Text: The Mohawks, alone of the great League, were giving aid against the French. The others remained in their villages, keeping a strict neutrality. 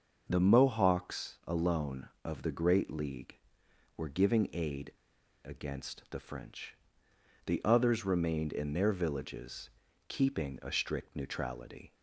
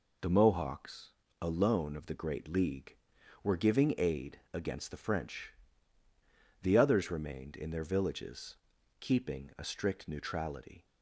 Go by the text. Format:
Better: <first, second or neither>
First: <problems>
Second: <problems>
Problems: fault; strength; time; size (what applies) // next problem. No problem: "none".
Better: second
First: starts louder than the rest; until 1.3 s; 6 dB // pauses between "aid" and "against"; noticeable; at 4.9 s; 0.53 s long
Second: none